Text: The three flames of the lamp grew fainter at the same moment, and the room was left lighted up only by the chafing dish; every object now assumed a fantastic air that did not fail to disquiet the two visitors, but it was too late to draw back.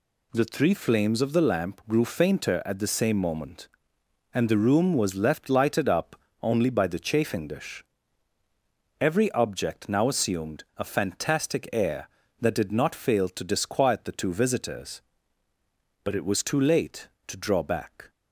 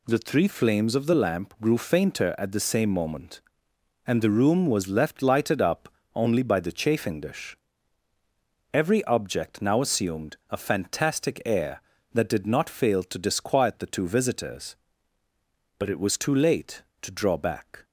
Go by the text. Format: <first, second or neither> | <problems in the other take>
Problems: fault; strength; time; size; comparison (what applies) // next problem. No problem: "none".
neither | pauses between "up" and "only"; slight; the same in both // pauses between "assumed" and "a"; slight; the same in both